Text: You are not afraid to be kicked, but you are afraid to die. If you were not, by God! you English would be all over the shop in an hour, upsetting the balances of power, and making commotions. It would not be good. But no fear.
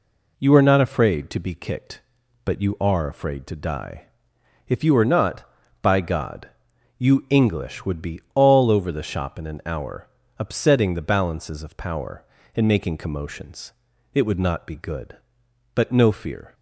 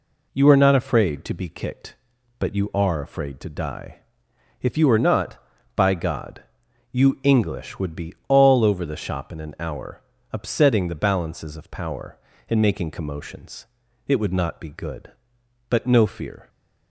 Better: neither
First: pauses between "be" and "all"; slight; at 8.1 s; 0.16 s long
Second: pauses between "be" and "all"; slight; at 8.1 s; 0.16 s long

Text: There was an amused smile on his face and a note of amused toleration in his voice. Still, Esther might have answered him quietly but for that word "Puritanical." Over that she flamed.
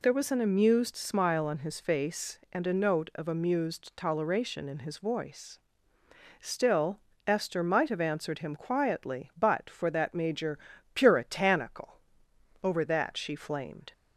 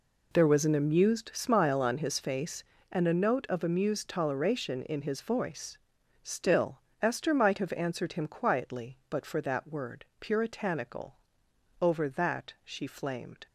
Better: second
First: says "major" for "word"; at 10.1 s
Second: none

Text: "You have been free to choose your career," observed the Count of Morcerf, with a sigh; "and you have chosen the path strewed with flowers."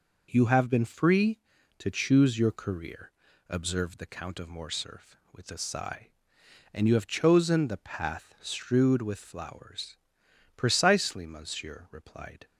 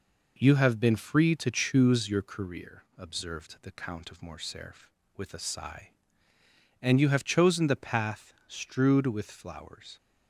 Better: second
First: goes on to say "Precisely monsieur replied"; strong; from 10.5 s on; 1.9 s long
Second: none

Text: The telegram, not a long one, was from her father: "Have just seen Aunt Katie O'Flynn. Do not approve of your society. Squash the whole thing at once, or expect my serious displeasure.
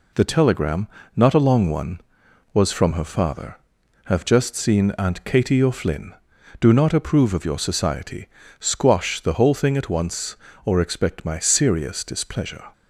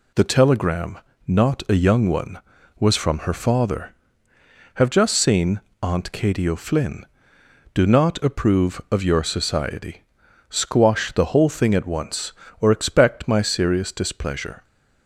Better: first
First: none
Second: says "young" for "long"; at 1.7 s // pauses between "seen" and "Aunt"; slight; at 5.5 s; 0.24 s long

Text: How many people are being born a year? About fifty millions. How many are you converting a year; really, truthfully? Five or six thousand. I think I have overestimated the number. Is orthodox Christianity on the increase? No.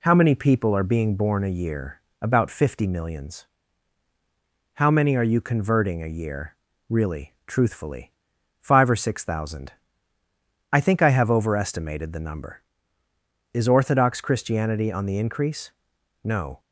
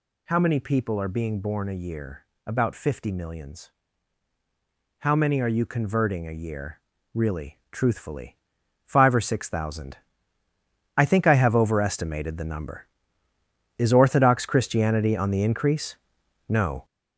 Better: first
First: none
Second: gets louder; strong; throughout; 7.5 dB

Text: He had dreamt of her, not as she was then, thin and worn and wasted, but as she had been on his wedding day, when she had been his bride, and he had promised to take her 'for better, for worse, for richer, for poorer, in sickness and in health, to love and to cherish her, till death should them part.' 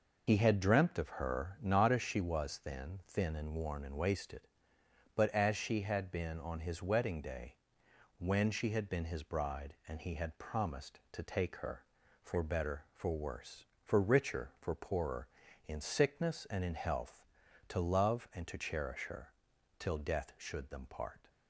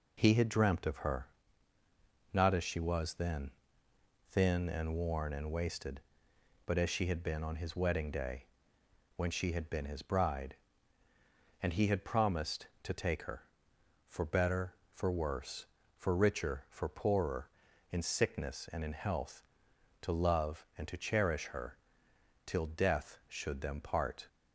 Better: second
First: loses the start of "He"; at 0.2 s; 35 ms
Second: none

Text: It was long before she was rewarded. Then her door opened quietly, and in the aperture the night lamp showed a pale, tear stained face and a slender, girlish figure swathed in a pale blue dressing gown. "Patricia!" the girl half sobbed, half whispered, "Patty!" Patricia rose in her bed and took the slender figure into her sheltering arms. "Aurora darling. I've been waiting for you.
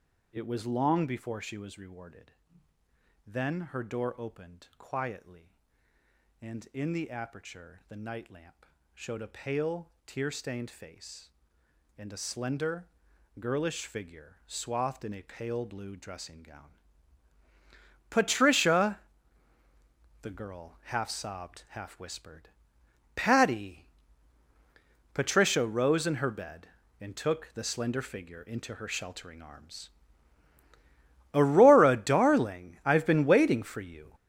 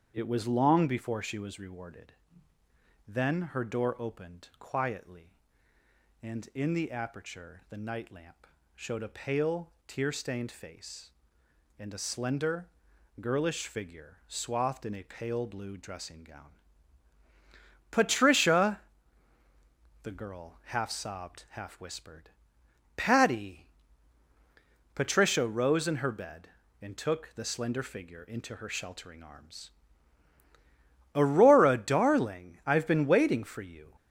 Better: second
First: gets louder; strong; throughout; 9.5 dB // starts louder than the rest; until 1.3 s; 7 dB // pauses between "lamp" and "showed"; slight; at 8.6 s; 0.30 s long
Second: starts louder than the rest; strong; until 1.1 s; 8 dB // pauses between "lamp" and "showed"; slight; at 8.4 s; 0.30 s long

